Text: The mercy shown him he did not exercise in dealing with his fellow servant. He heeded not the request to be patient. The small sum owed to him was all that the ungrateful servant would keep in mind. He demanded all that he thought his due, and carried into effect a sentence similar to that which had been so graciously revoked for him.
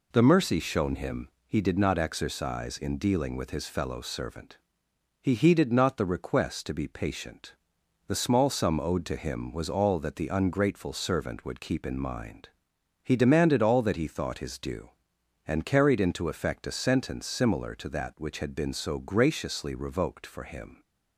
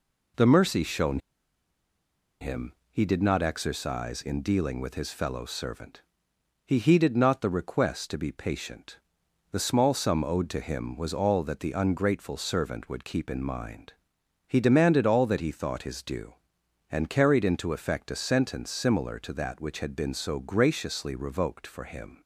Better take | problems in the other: first | pauses between "shown" and "him"; at 1.1 s; 1.2 s long // pauses between "him" and "he"; slight; at 2.7 s; 0.18 s long; slight in the first

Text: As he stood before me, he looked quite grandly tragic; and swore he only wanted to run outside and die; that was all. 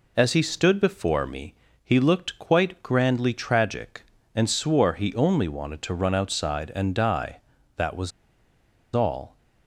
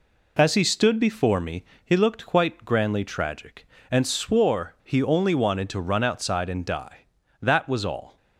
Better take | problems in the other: second | pauses between "was" and "all"; noticeable; at 8.1 s; 0.84 s long

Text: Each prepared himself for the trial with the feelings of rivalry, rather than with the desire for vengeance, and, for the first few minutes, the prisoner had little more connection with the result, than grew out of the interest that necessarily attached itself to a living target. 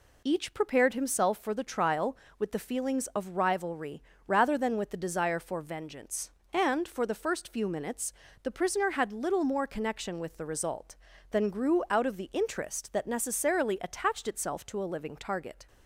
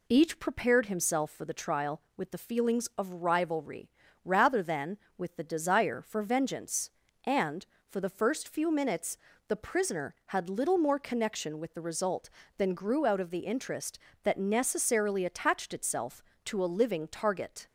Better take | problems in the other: neither | none

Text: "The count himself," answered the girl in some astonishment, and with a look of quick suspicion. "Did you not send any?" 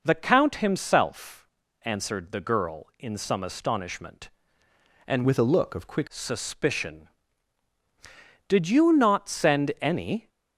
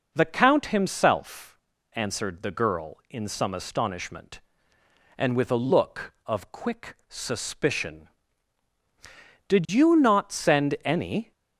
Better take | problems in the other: second | changes voice from "with" to "quick"; from 5.2 to 6.0 s; 0.8 s long

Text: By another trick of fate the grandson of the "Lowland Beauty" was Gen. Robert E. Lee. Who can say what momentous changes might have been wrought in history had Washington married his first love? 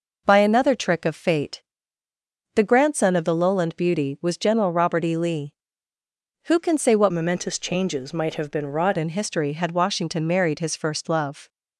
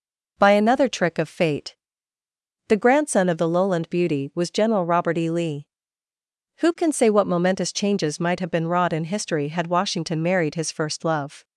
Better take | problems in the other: second | pauses between "fate" and "the"; noticeable; at 1.6 s; 0.94 s long; noticeable in the second // changes voice from "momentous" to "wrought"; from 7.1 to 8.9 s; 1.8 s long

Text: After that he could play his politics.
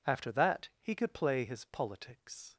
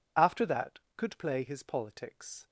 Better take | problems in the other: first | skips "he"; at 0.8 s

